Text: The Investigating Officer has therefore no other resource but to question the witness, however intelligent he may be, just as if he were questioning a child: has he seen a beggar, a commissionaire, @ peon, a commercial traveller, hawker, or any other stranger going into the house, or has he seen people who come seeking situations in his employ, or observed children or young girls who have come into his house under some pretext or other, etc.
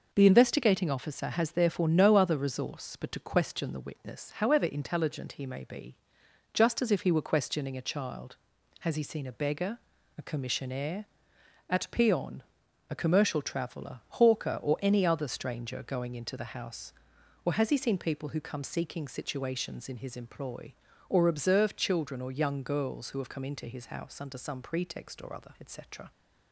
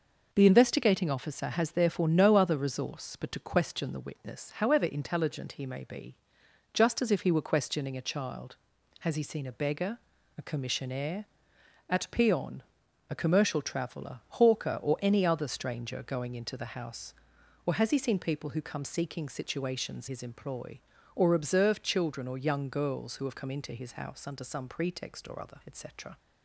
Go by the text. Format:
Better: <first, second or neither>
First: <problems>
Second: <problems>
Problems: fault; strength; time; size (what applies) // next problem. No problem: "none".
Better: first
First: none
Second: skips "in"; at 20.0 s